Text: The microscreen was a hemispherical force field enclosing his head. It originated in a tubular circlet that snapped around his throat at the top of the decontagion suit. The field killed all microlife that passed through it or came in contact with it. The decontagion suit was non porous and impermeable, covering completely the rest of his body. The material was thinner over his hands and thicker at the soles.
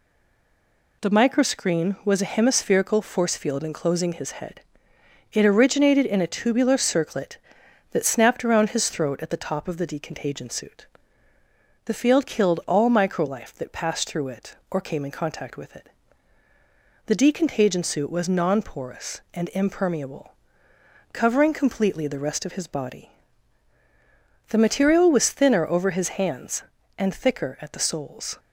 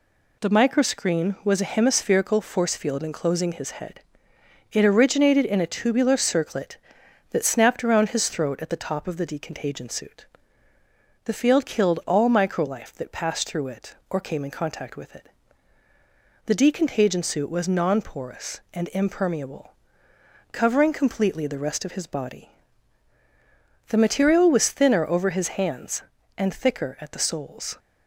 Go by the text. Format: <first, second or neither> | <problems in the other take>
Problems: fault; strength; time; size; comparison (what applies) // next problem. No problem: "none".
second | stays silent before the first word; until 1.0 s; 1.0 s long